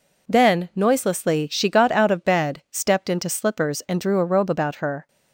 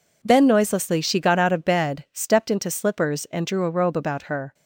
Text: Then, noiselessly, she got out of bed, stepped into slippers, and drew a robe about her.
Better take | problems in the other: neither | none

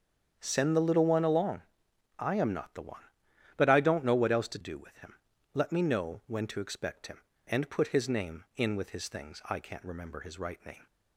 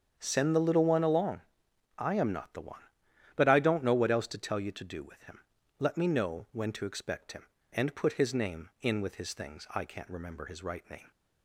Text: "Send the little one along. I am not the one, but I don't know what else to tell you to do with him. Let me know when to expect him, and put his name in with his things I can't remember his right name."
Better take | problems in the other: second | starts louder than the rest; strong; until 1.4 s; 8 dB; strong in the second // skips "tell you to"; at 4.5 s

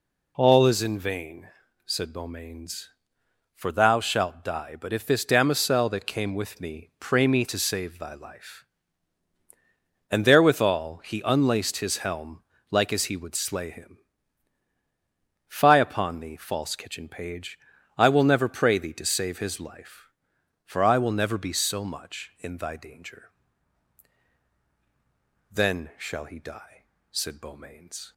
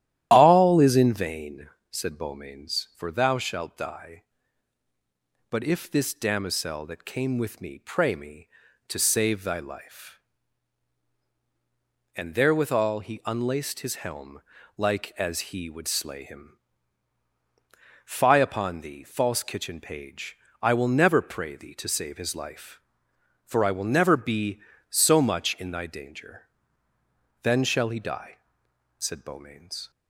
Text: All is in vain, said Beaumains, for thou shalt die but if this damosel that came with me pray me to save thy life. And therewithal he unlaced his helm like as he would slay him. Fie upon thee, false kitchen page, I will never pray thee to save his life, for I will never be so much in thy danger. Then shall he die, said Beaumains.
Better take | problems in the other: first | starts louder than the rest; strong; until 1.3 s; 12.5 dB // pauses between "helm" and "like"; at 14.4 s; 0.38 s long; slight in the first

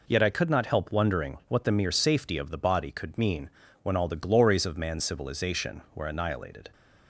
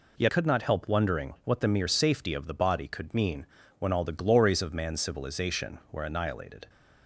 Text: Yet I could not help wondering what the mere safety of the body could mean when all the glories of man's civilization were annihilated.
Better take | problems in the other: first | skips "I"; at 0.2 s // pauses between "mean" and "when"; slight; at 3.4 s; 0.32 s long; slight in the first

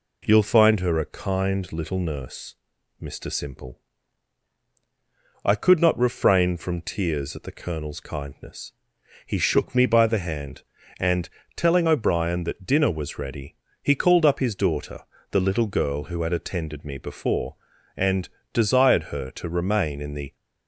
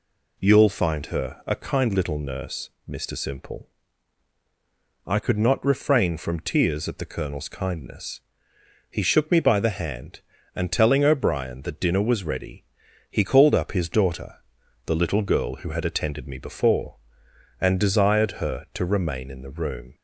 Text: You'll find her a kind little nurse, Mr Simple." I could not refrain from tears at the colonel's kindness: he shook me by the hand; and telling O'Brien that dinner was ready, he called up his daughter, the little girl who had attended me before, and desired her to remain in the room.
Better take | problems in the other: second | pauses between "and" and "telling"; slight; at 11.2 s; 0.30 s long // pauses between "and" and "desired"; slight; at 18.2 s; 0.24 s long // stops before "room"; at 20.3 s

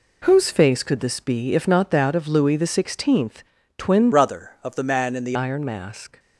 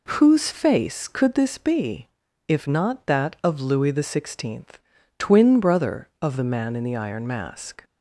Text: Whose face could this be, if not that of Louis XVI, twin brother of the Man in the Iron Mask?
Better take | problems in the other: second | changes voice from "brother" to "the"; from 4.1 to 5.3 s; 1.2 s long

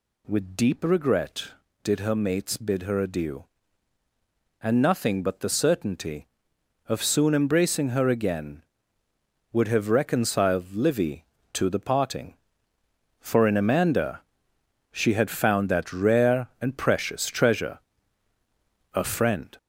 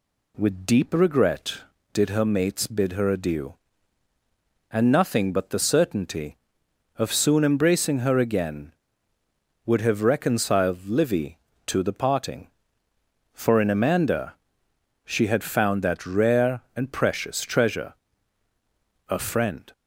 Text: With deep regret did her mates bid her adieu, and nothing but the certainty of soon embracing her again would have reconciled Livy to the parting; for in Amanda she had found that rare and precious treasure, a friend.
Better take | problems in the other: second | gets louder; noticeable; throughout; 5.5 dB // pauses between "Amanda" and "she"; noticeable; at 14.2 s; 0.70 s long; noticeable in the second

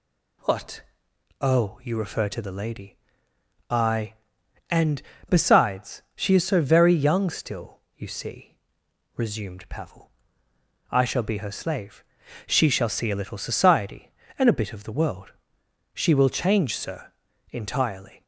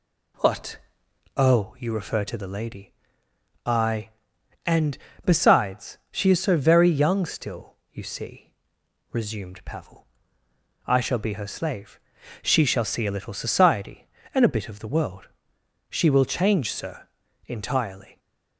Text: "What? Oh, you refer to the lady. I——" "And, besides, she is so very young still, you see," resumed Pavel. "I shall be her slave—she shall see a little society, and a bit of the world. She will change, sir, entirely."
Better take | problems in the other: first | starts louder than the rest; slight; until 1.7 s; 2 dB

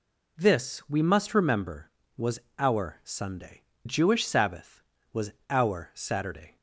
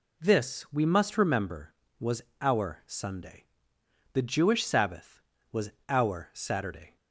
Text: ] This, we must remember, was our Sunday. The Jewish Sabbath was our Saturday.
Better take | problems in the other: second | pauses between "was" and "our"; slight; at 2.3 s; 0.18 s long; slight in the second // skips "The"; at 3.7 s // pauses between "was" and "our"; slight; at 5.3 s; 0.18 s long; slight in the second

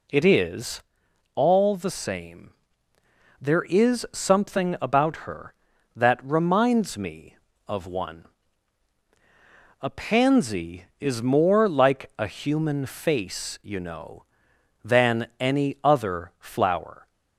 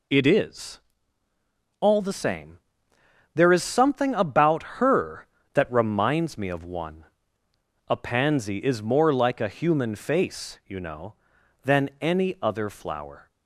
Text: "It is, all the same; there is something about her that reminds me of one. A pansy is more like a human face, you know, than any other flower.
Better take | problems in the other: neither | none

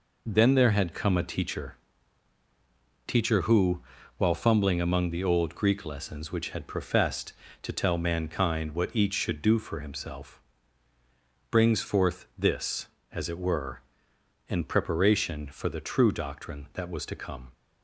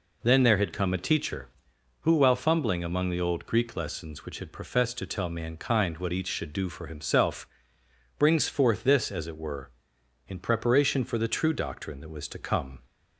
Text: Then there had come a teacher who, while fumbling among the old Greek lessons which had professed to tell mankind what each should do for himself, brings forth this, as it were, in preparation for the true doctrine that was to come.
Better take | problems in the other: second | says "teacher" twice; at 3.0 s

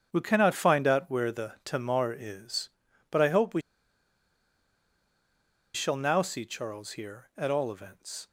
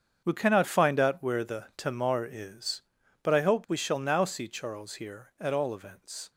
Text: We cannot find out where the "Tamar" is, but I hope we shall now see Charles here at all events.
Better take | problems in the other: second | starts louder than the rest; strong; until 1.1 s; 7.5 dB; strong in the second // pauses between "we" and "shall"; strong; at 3.6 s; 2.1 s long

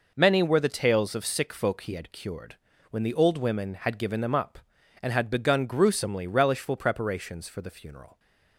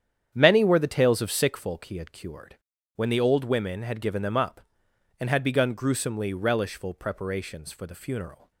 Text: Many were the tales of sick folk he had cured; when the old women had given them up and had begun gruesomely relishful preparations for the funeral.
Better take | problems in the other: first | starts louder than the rest; strong; until 1.7 s; 9 dB

